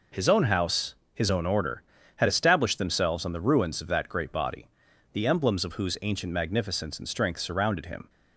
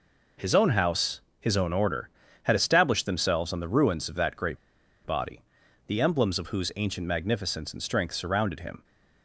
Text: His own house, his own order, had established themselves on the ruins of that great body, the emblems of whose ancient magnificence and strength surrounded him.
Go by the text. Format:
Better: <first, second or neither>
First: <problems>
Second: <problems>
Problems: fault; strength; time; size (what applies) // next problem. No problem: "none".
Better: first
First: none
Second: pauses between "great" and "body"; noticeable; at 4.5 s; 0.47 s long